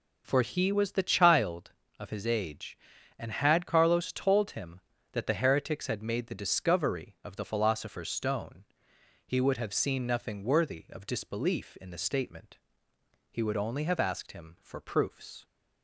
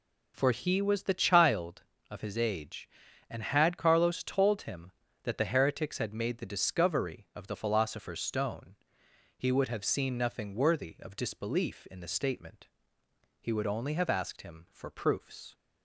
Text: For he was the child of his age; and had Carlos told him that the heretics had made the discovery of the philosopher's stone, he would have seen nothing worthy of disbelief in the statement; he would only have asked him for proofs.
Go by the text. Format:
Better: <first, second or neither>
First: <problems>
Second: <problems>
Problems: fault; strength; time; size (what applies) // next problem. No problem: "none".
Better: neither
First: none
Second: none